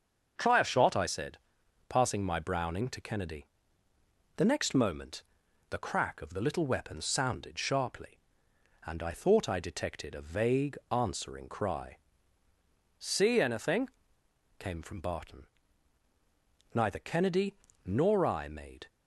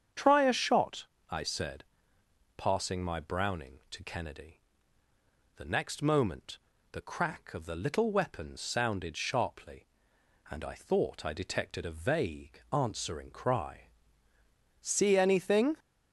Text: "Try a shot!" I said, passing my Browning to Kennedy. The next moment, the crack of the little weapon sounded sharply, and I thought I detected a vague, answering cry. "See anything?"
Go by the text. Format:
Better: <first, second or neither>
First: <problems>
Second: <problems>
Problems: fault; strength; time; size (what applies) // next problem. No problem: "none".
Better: second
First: starts louder than the rest; until 1.3 s; 6.5 dB // goes on to say "came from Barton Neither Kennedy nor I made"; strong; from 14.5 s on; 4.3 s long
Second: starts louder than the rest; strong; until 1.3 s; 8 dB